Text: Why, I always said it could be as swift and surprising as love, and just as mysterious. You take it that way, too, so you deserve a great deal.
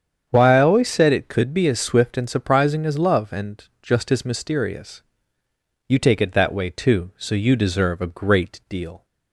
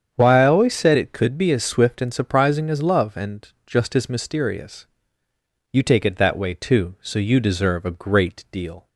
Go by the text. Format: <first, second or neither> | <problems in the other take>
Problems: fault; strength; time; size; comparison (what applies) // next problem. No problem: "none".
neither | starts louder than the rest; strong; the same in both // pauses between "and" and "just"; slight; the same in both